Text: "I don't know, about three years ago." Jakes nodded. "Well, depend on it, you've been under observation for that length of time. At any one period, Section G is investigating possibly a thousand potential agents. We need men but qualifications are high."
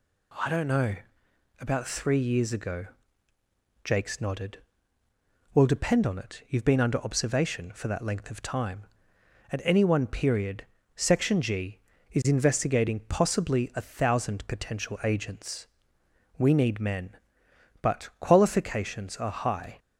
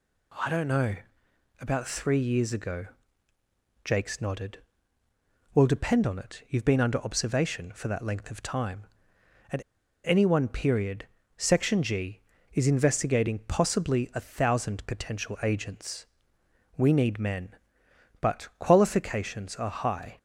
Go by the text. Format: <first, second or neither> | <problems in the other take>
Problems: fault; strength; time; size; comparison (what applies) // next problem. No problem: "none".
first | pauses between "At" and "any"; at 9.6 s; 0.43 s long